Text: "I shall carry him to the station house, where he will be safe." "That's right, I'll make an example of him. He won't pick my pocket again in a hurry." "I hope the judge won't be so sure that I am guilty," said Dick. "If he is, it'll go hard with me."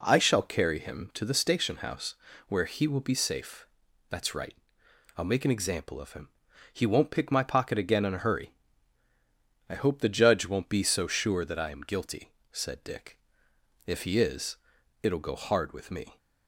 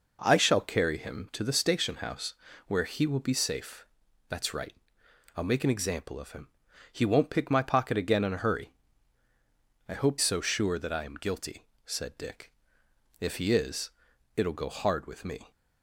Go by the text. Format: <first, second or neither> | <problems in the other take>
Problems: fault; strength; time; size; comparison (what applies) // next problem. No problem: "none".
first | skips "the judge won't be"; at 10.1 s